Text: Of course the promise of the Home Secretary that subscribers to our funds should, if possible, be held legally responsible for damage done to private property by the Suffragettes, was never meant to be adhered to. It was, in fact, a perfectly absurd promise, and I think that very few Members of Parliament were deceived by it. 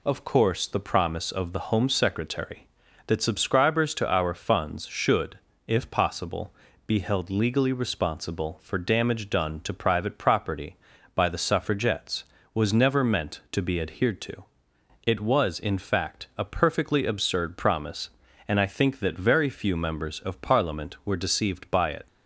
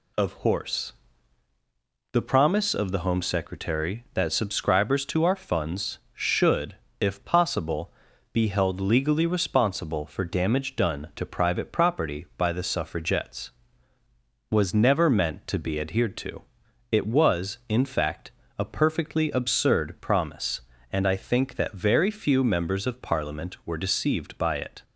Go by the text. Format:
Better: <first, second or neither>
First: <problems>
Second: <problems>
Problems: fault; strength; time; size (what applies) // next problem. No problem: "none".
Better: first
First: none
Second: says "horse" for "course"; at 0.4 s